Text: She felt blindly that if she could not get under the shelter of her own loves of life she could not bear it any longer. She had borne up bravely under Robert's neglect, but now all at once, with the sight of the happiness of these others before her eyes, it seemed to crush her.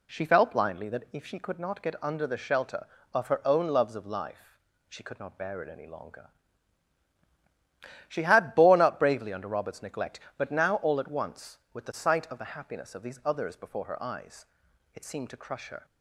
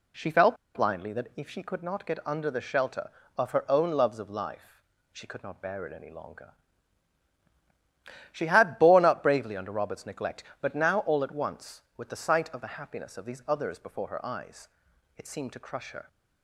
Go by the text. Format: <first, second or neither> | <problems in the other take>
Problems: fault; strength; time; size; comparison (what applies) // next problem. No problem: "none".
first | pauses between "felt" and "blindly"; slight; at 0.5 s; 0.19 s long // pauses between "life" and "she"; slight; at 4.8 s; 0.30 s long; slight in the first